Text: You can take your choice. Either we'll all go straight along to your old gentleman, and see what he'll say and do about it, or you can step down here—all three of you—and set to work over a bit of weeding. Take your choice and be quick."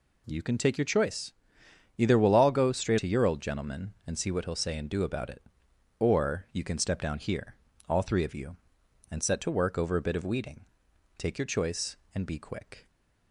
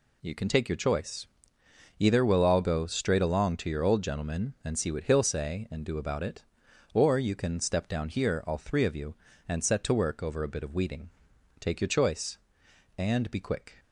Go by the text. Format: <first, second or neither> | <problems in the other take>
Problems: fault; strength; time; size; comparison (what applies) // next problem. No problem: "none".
second | skips "along"; at 2.9 s